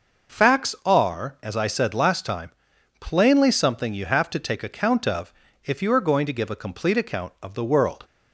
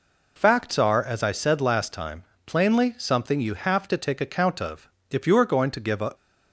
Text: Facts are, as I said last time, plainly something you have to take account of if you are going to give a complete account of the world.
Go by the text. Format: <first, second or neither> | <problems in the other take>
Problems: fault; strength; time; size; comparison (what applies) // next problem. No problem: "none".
first | pauses between "of" and "if"; slight; at 4.8 s; 0.22 s long; slight in the first // stops before "complete account of the world"; at 6.1 s